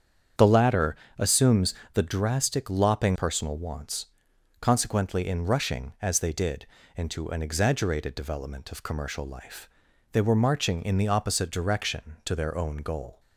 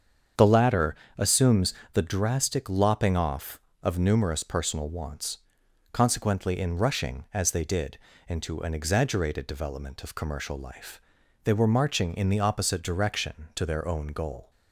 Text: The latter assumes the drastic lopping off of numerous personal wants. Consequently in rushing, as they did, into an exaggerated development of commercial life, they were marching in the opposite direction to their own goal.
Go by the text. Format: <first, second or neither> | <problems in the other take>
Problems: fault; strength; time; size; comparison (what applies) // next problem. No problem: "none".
second | starts louder than the rest; strong; until 1.5 s; 8 dB; strong in the second // pauses between "latter" and "assumes"; slight; at 0.9 s; 0.22 s long; slight in the second // pauses between "assumes" and "the"; slight; at 1.7 s; 0.22 s long; slight in the second // skips "off of numerous"; at 3.1 s